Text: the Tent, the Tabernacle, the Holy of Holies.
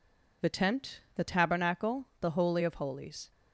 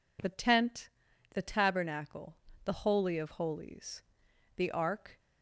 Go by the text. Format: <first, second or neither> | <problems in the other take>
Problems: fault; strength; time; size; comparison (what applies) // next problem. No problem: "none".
first | goes on to say "The Ark"; noticeable; from 4.5 s on; 0.62 s long